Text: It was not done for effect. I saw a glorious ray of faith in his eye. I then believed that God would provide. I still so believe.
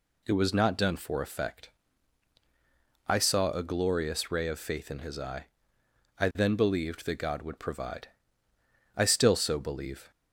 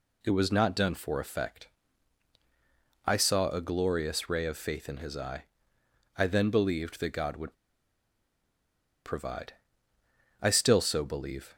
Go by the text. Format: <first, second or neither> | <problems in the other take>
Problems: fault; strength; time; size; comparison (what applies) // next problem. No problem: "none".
first | pauses between "would" and "provide"; strong; at 7.5 s; 1.5 s long